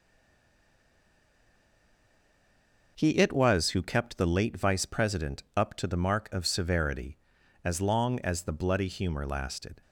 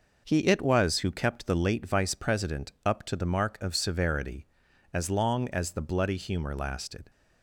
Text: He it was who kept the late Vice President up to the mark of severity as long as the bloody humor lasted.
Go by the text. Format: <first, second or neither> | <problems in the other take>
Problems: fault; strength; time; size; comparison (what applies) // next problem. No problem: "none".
second | stays silent before the first word; strong; until 2.9 s; 2.9 s long